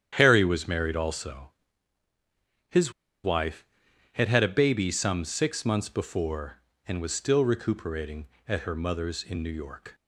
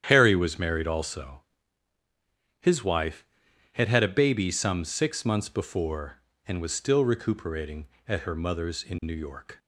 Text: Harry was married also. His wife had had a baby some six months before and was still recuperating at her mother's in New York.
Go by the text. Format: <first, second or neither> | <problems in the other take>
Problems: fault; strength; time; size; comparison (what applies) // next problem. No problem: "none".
second | starts louder than the rest; strong; until 1.1 s; 9.5 dB; strong in the second // pauses between "His" and "wife"; slight; at 2.9 s; 0.32 s long